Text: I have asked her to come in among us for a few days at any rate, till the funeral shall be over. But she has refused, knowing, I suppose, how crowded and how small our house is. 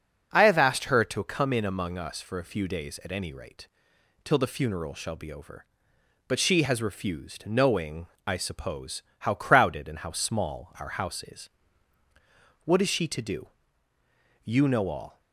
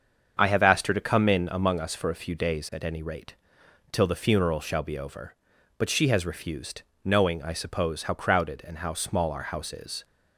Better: second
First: starts louder than the rest; until 1.3 s; 6 dB // goes on to say "What is she to do You know all"; strong; from 12.6 s on; 2.5 s long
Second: starts louder than the rest; until 1.4 s; 7 dB

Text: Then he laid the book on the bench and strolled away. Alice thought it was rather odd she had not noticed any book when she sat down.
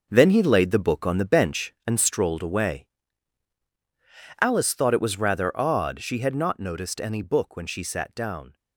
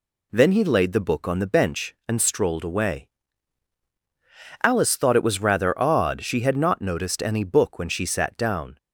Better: second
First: gets quieter; strong; throughout; 9 dB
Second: none

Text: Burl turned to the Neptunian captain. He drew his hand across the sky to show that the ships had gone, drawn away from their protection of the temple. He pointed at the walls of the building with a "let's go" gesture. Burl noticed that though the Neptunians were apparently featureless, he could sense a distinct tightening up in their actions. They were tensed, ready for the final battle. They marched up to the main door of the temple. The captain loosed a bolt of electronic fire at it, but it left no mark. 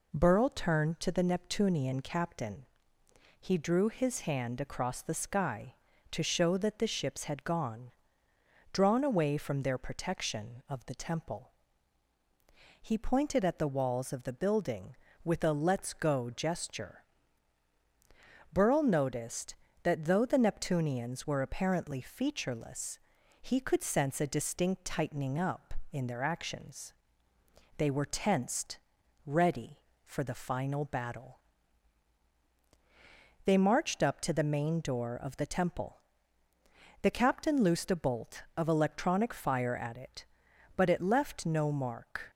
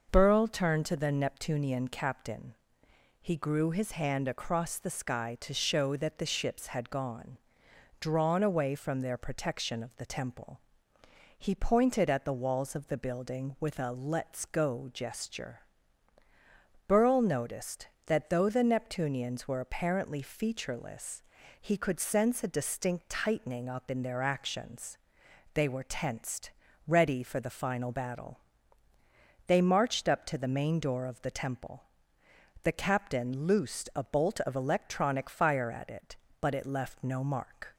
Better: first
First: none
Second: starts louder than the rest; noticeable; until 1.1 s; 6 dB // says "grew" for "drew"; at 3.3 s

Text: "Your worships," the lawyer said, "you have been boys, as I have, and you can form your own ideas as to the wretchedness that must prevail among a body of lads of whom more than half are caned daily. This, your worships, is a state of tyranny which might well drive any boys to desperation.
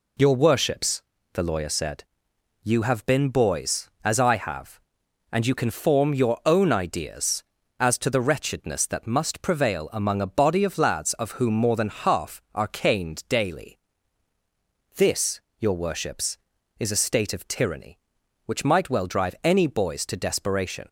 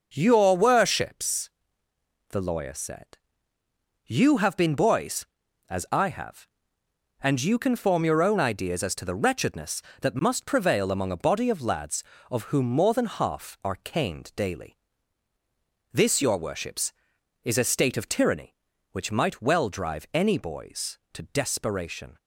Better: neither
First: none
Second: none

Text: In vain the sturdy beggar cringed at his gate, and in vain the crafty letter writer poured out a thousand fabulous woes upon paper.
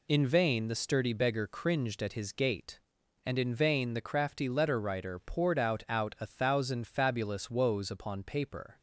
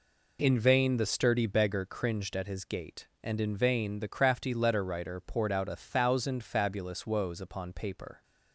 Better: second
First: says "out" twice; at 5.8 s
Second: none

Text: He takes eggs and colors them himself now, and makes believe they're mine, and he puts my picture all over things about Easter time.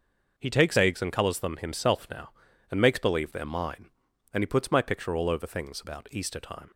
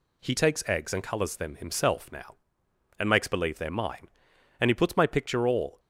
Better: first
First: none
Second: stops before "over things about Easter time"; at 5.7 s

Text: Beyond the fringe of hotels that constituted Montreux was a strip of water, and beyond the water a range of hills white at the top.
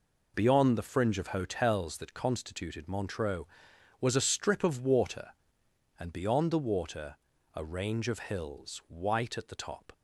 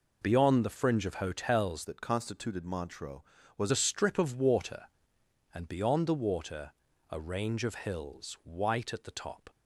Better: first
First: pauses between "water" and "a"; at 7.1 s; 0.40 s long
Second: changes voice from "that" to "was"; from 1.8 to 3.7 s; 1.9 s long // pauses between "water" and "a"; at 6.6 s; 0.40 s long

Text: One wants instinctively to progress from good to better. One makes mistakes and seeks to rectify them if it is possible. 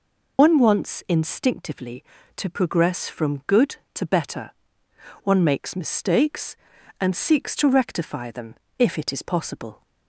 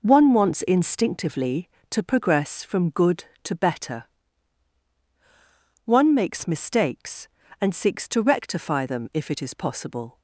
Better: second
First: loses the start of "One"; at 0.3 s; 90 ms // pauses between "them" and "if"; slight; at 8.5 s; 0.24 s long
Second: none

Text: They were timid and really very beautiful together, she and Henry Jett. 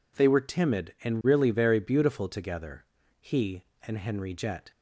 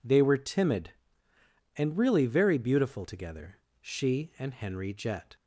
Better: second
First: says "he" for "she"; at 3.1 s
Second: none

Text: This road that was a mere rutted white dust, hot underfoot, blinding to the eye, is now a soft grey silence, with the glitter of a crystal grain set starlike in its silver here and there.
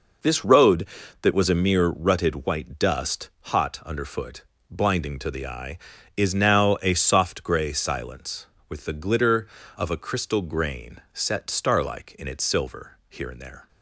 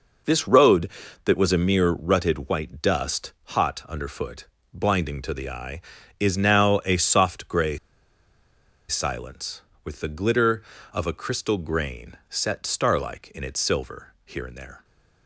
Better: first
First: pauses between "grain" and "set"; slight; at 10.9 s; 0.16 s long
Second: pauses between "grey" and "silence"; at 7.7 s; 1.1 s long // pauses between "grain" and "set"; slight; at 12.1 s; 0.16 s long

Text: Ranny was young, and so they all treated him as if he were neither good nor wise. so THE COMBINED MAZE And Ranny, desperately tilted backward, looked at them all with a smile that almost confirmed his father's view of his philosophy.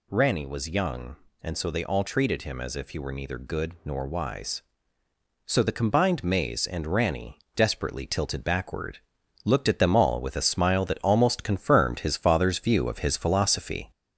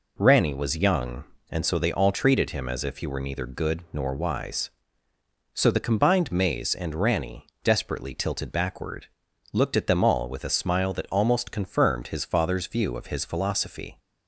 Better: second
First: gets louder; slight; throughout; 3 dB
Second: none

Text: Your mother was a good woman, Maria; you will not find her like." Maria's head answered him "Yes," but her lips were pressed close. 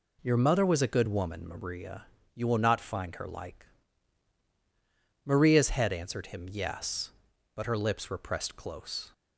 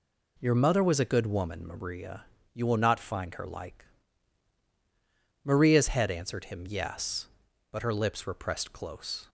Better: neither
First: none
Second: none

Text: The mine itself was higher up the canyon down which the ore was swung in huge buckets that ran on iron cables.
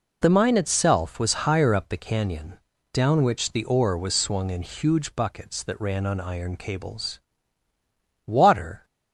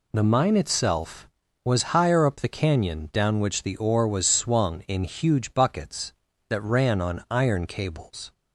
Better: second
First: pauses between "canyon" and "down"; slight; at 2.6 s; 0.32 s long // goes on to say "Water"; noticeable; from 8.2 s on; 0.62 s long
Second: none

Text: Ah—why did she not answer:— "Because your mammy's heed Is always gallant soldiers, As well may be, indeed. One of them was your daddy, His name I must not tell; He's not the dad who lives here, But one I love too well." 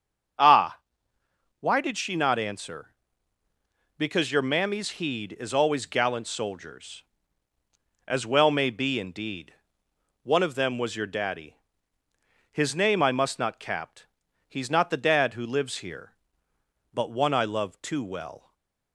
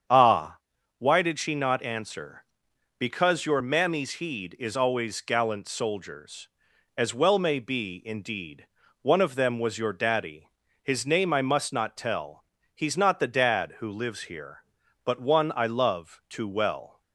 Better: second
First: starts louder than the rest; until 2.2 s; 7 dB // says "capt" for "tell"; at 13.5 s // stays silent after the last word; slight; from 18.3 s on; 0.6 s long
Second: starts louder than the rest; strong; until 1.4 s; 8 dB

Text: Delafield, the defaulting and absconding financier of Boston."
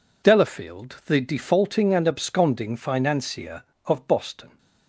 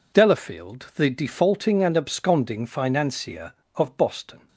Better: neither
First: none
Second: none

